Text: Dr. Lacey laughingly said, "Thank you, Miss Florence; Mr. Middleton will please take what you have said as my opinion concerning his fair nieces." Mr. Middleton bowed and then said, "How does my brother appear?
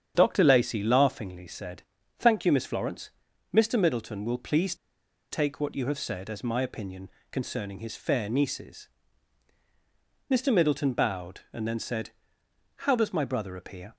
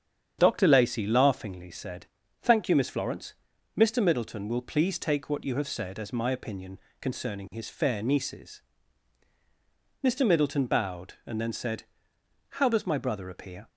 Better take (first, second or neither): second